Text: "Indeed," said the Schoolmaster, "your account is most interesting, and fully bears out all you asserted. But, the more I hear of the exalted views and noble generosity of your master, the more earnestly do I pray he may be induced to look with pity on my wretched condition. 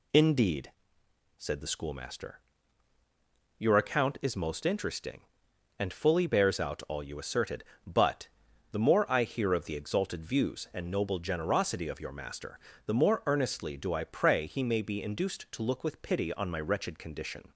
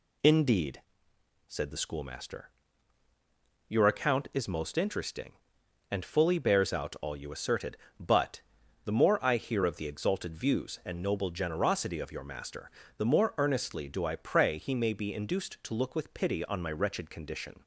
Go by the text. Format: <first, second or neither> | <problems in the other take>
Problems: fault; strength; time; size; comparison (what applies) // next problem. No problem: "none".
neither | none